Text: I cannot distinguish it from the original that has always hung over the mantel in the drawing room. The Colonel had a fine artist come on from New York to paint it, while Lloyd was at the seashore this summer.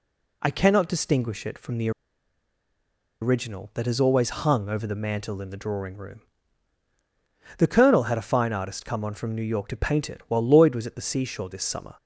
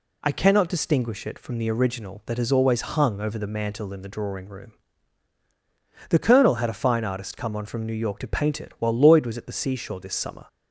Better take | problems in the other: second | pauses between "the" and "original"; strong; at 1.8 s; 1.3 s long

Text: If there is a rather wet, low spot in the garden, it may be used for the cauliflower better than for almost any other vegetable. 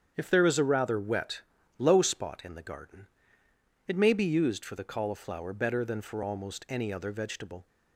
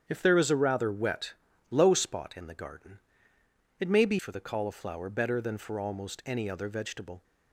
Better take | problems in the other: first | starts louder than the rest; strong; until 1.0 s; 8.5 dB; strong in the first // skips "used"; at 4.1 s

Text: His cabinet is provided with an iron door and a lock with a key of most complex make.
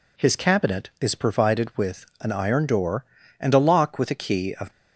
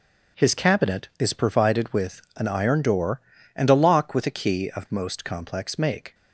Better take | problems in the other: second | stops before "most complex make"; at 4.7 s

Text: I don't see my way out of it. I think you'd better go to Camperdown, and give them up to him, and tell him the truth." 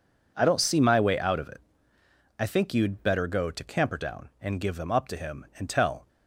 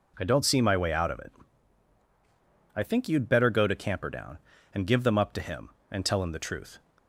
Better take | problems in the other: second | stops before "him the truth"; at 6.0 s

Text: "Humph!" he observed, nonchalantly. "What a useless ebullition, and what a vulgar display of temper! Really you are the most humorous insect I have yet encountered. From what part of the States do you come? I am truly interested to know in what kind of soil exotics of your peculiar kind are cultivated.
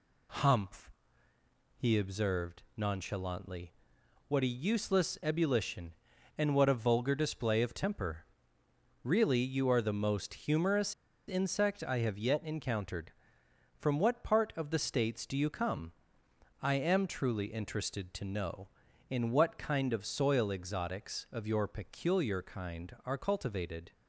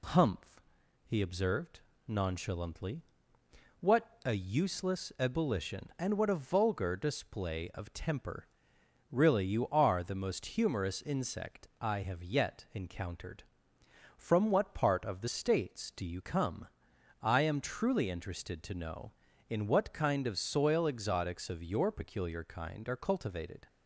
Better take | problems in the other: second | pauses between "humorous" and "insect"; slight; at 10.9 s; 0.34 s long

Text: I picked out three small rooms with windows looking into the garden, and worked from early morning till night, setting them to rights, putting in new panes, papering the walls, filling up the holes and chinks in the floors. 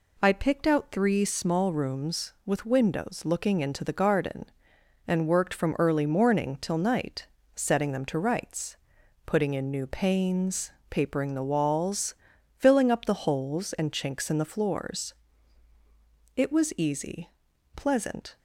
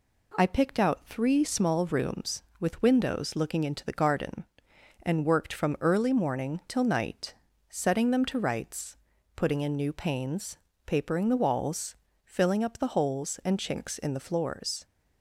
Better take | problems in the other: second | goes on to say "It was easy pleasant"; strong; from 16.3 s on; 2.0 s long

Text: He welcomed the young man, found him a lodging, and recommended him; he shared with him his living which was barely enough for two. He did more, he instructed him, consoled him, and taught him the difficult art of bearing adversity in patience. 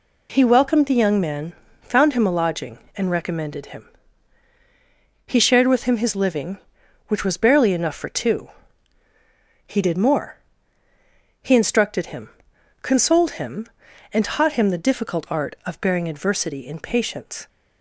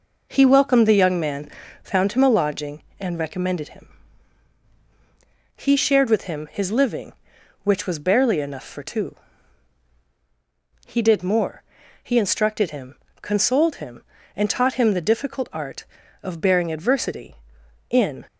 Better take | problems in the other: first | stops before "patience"; at 18.2 s

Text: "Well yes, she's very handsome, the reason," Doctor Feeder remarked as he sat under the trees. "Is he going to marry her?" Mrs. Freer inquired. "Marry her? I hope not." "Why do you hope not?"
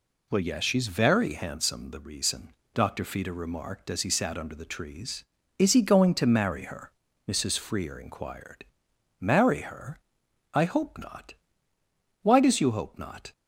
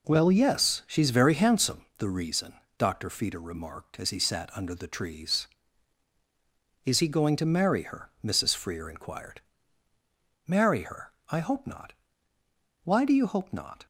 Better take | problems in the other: second | says "does" for "do"; at 12.4 s

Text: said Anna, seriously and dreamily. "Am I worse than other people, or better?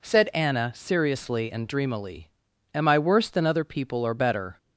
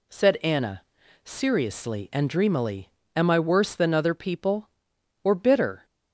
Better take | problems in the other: first | says "bitter" for "better"; at 5.3 s

